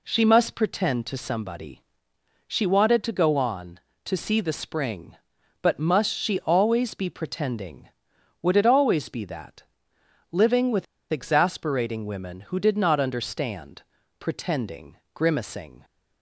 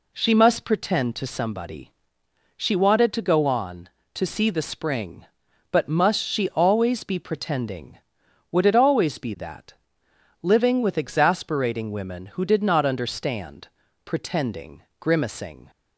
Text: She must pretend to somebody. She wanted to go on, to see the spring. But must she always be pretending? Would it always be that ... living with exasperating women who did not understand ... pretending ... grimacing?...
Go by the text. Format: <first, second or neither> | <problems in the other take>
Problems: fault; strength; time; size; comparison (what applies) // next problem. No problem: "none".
second | pauses between "with" and "exasperating"; slight; at 10.8 s; 0.27 s long